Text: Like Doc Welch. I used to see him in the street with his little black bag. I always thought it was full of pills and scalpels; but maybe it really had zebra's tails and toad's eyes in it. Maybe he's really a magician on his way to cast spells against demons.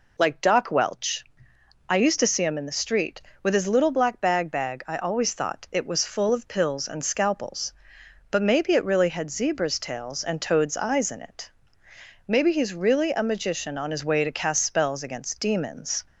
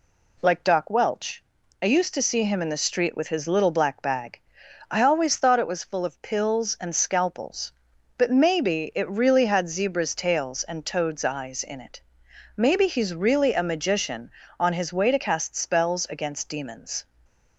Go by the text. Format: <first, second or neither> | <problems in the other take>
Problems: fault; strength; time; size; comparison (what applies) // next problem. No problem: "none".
second | says "bag" twice; at 4.5 s